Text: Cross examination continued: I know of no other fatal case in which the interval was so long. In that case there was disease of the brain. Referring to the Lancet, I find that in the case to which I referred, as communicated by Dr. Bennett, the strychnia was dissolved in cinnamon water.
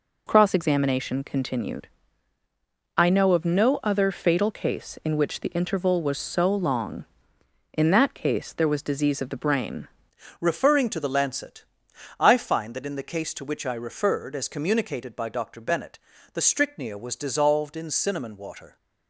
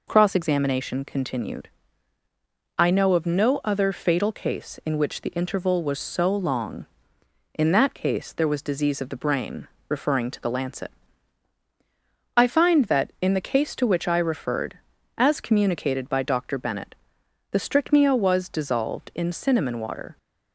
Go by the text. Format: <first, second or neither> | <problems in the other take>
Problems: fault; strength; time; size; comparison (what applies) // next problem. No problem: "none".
second | changes voice at "Referring"; from 10.3 s on; 8.4 s long